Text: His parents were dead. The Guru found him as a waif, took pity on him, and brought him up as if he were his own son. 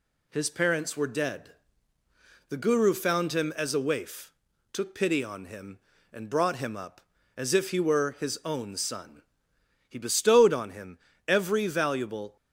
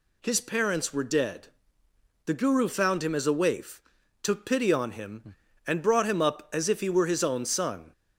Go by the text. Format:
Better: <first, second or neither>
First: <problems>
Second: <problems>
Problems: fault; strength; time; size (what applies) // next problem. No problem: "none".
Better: second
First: goes on to say "He bestowed on him every valuable"; strong; from 9.8 s on; 2.4 s long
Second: none